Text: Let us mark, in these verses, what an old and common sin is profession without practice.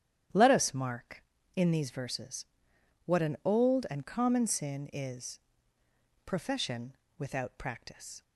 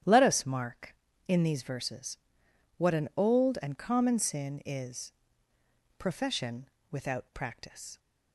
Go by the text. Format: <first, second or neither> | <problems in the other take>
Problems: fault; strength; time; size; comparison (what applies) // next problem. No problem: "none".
neither | starts louder than the rest; strong; the same in both // pauses between "is" and "profession"; noticeable; the same in both // pauses between "profession" and "without"; slight; the same in both